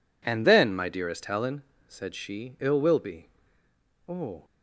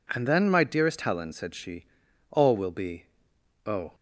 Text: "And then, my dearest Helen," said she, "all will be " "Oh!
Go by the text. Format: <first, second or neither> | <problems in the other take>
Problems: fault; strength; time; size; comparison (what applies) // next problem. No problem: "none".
second | says "ill" for "all"; at 2.6 s